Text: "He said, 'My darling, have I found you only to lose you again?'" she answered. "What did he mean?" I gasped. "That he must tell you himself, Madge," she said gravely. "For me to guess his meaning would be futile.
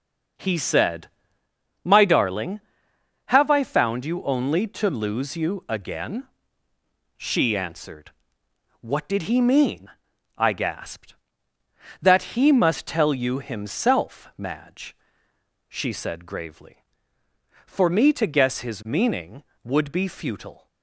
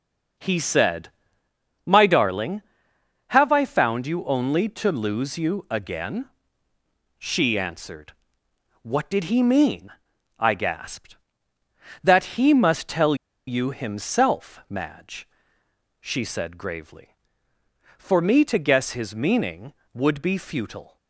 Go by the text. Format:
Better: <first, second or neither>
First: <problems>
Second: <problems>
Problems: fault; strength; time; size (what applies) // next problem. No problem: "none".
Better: first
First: none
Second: pauses between "tell" and "you"; slight; at 13.1 s; 0.32 s long